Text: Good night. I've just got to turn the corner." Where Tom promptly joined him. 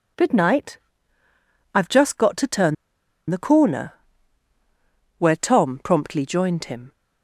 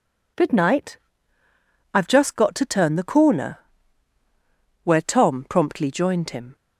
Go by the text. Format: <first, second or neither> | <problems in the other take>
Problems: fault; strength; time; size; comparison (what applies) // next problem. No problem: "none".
second | pauses between "turn" and "the"; noticeable; at 2.7 s; 0.54 s long